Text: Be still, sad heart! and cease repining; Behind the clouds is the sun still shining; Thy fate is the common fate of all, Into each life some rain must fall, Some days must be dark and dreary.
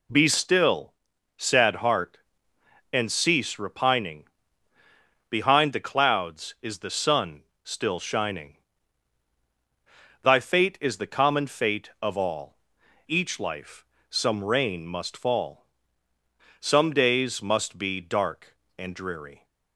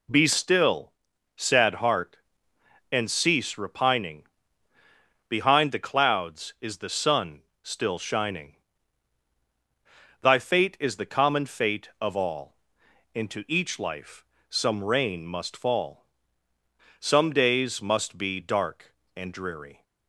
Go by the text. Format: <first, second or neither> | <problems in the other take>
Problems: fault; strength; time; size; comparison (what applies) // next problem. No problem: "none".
second | pauses between "sun" and "still"; slight; at 7.4 s; 0.20 s long; slight in the second // skips "Into"; at 12.8 s // pauses between "life" and "some"; slight; at 13.8 s; 0.24 s long; slight in the second